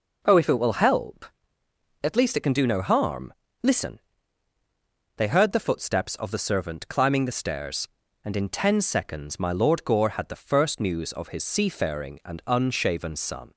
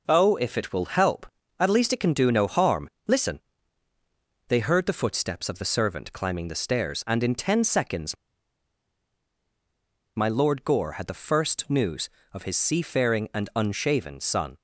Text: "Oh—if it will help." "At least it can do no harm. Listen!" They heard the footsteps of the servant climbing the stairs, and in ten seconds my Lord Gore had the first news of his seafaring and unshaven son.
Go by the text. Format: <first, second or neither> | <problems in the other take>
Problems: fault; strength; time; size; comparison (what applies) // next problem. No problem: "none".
first | pauses between "seconds" and "my"; strong; at 8.1 s; 2.0 s long